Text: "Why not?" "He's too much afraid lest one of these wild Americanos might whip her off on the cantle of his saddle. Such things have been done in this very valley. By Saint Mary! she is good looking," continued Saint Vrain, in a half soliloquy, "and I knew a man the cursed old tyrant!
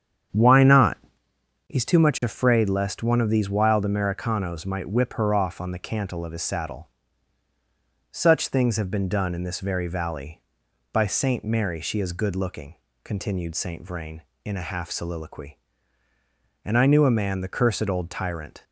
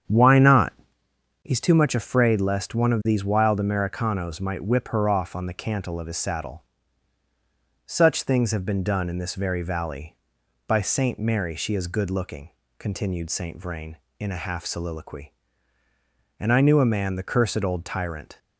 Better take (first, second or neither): neither